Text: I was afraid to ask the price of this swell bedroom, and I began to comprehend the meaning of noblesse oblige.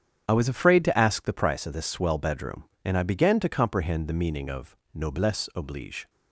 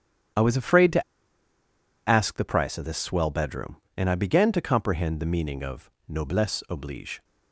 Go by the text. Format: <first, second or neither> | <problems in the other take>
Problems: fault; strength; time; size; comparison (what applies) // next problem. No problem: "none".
first | starts louder than the rest; strong; until 2.4 s; 9 dB; strong in the first // pauses between "to" and "ask"; at 1.0 s; 1.0 s long // pauses between "of" and "noblesse"; slight; at 5.8 s; 0.18 s long; slight in the first